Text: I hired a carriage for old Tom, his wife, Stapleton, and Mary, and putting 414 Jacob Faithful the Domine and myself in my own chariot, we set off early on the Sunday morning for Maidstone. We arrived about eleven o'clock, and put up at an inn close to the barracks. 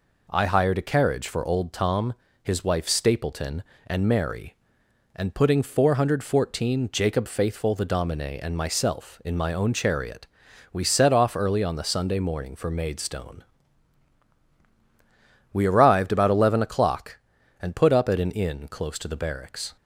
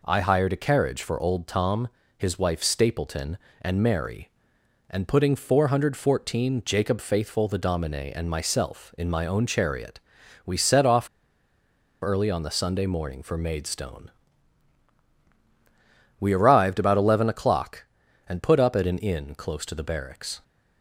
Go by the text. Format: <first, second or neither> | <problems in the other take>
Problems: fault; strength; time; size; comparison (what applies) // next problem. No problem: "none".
first | pauses between "off" and "early"; noticeable; at 11.0 s; 0.94 s long